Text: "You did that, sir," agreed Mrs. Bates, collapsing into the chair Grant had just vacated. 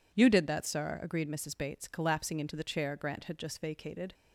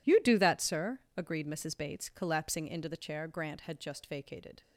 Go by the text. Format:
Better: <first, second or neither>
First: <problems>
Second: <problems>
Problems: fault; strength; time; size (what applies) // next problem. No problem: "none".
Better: first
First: none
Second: says "do" for "did"; at 0.1 s